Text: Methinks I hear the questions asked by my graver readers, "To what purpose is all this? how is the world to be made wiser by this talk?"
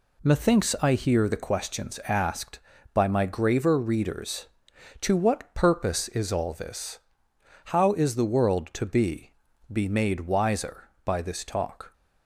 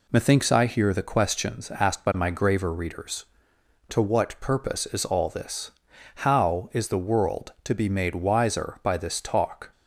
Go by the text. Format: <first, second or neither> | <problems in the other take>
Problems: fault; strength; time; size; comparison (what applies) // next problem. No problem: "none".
second | says "be" twice; at 9.7 s